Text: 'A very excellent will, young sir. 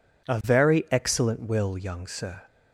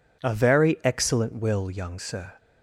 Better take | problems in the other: neither | none

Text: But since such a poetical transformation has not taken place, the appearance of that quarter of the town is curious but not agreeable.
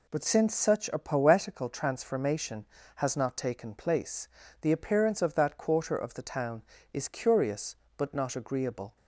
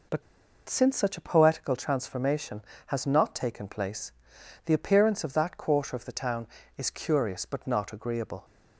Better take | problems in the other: first | pauses between "But" and "since"; noticeable; at 0.2 s; 0.46 s long

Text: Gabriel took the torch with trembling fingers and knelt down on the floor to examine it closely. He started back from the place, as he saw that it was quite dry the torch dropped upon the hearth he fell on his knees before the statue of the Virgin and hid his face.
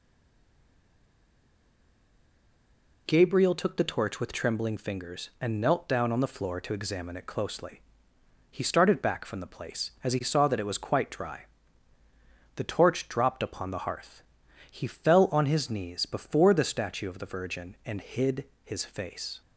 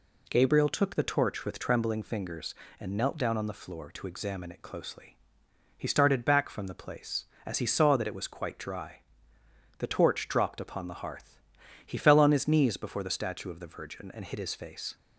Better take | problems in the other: second | stays silent before the first word; strong; until 3.0 s; 3.0 s long // pauses between "dry" and "the"; at 11.4 s; 1.1 s long; noticeable in the second // pauses between "hearth" and "he"; noticeable; at 14.2 s; 0.48 s long; noticeable in the second // pauses between "hid" and "his"; slight; at 18.4 s; 0.18 s long

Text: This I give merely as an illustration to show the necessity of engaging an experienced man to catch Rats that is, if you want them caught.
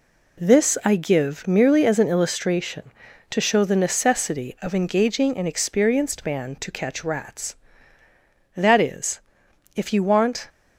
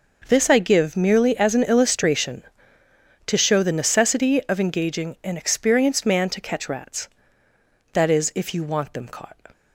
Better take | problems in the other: second | stops before "them caught"; at 10.4 s

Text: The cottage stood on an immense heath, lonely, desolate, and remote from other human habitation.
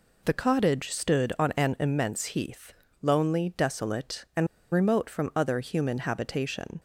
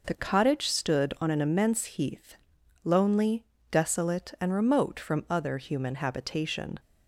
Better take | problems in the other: second | pauses between "and" and "remote"; slight; at 4.4 s; 0.25 s long

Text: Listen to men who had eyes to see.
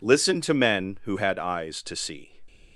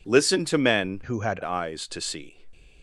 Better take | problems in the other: first | changes voice from "who" to "had"; from 1.0 to 1.4 s; 0.4 s long

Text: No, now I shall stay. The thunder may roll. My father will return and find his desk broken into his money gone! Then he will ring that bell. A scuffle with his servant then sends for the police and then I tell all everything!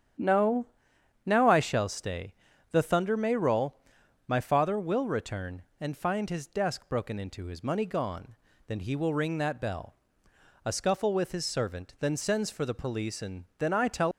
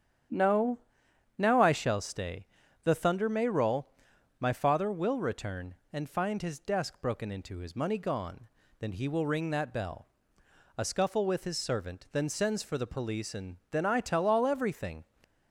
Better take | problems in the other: second | starts louder than the rest; strong; until 1.7 s; 9 dB; strong in the second // pauses between "and" and "then"; slight; at 13.4 s; 0.16 s long; slight in the second // stops before "all everything"; at 14.1 s

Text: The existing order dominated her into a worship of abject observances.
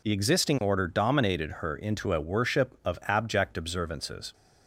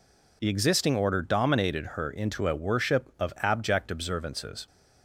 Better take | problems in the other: neither | none

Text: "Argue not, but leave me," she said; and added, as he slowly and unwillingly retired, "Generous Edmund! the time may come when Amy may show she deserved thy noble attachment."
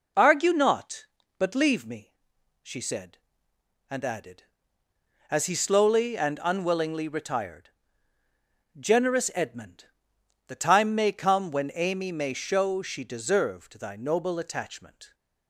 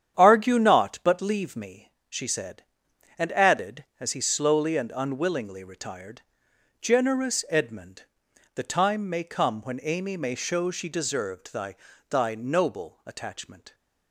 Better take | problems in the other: first | starts louder than the rest; strong; until 1.1 s; 9 dB // says "thy" twice; at 12.1 s

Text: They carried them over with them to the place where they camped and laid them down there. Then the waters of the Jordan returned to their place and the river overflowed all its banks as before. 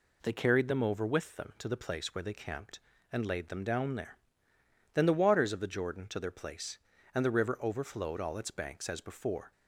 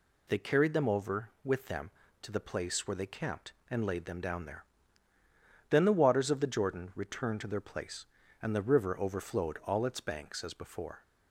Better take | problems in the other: second | skips "returned"; at 6.0 s

